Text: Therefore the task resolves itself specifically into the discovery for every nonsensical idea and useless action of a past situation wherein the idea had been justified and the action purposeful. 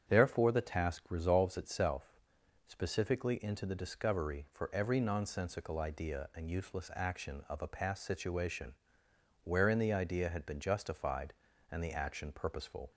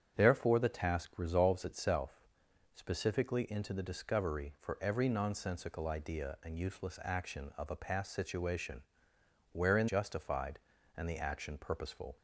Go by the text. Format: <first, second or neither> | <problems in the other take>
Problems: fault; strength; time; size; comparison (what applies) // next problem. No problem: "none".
first | starts louder than the rest; strong; until 1.2 s; 8 dB; strong in the first // pauses between "itself" and "specifically"; noticeable; at 2.2 s; 0.52 s long; noticeable in the first // pauses between "situation" and "wherein"; noticeable; at 8.8 s; 0.70 s long; noticeable in the first // skips "the idea had been"; at 9.8 s